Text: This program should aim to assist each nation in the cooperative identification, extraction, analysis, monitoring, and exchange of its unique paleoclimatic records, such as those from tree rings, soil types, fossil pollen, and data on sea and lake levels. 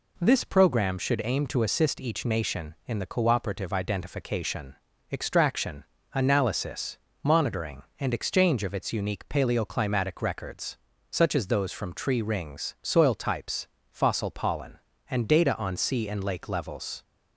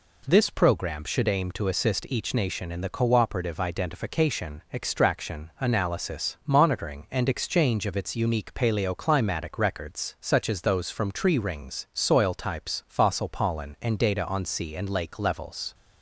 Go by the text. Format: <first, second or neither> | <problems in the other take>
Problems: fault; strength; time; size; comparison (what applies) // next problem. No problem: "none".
neither | none